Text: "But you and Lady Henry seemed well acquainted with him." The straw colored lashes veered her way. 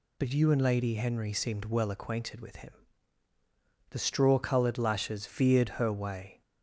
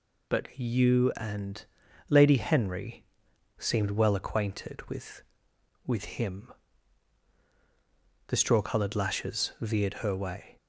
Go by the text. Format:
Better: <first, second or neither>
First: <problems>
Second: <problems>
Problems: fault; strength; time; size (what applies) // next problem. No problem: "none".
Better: first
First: none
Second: pauses between "and" and "Lady"; noticeable; at 1.6 s; 0.46 s long // pauses between "Henry" and "seemed"; noticeable; at 3.0 s; 0.54 s long // says "with" twice; at 5.8 s